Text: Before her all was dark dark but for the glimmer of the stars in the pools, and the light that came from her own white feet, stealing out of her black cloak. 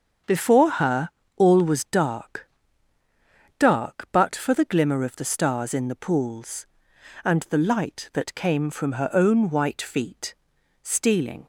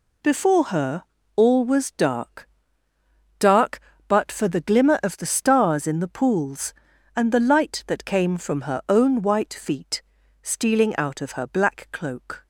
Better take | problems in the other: second | starts louder than the rest; until 1.5 s; 7 dB // pauses between "her" and "all"; slight; at 1.0 s; 0.26 s long; slight in the second // pauses between "dark" and "dark"; at 2.4 s; 1.1 s long; noticeable in the second // stops before "out of her black cloak"; at 11.4 s

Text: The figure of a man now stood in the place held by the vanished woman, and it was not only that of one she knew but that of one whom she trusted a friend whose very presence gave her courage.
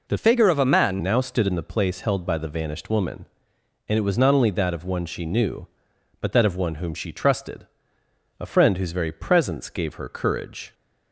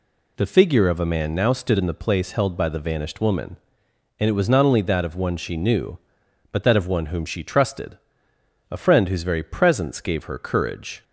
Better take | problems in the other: second | changes voice from "figure" to "man"; from 0.1 to 1.0 s; 0.9 s long // pauses between "trusted" and "a"; noticeable; at 7.6 s; 0.74 s long; noticeable in the second

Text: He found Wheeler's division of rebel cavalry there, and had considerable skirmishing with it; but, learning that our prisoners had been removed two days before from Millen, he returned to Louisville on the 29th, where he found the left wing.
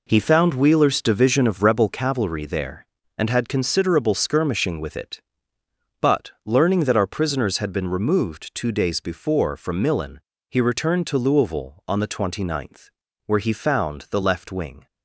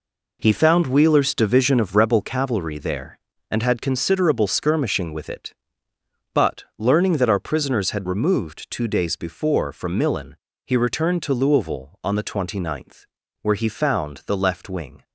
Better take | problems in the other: first | skips "been"; at 8.0 s

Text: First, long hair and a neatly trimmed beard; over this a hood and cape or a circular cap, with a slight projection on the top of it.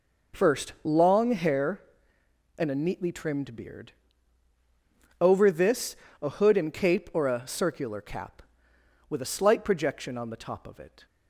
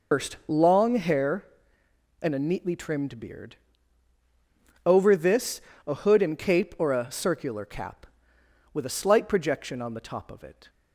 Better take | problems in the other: first | loses the start of "First"; at 0.1 s; 140 ms // pauses between "this" and "a"; slight; at 5.6 s; 0.28 s long; slight in the first

